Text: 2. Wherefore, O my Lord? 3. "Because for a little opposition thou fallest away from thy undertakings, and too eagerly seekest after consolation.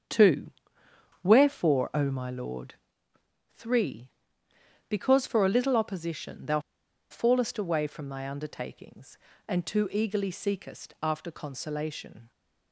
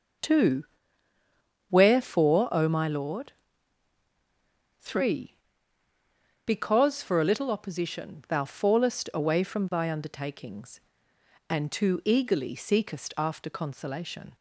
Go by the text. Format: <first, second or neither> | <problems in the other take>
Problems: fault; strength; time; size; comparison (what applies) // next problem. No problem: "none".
second | starts louder than the rest; strong; until 1.7 s; 7.5 dB; also in the second // pauses between "thou" and "fallest"; noticeable; at 6.5 s; 0.50 s long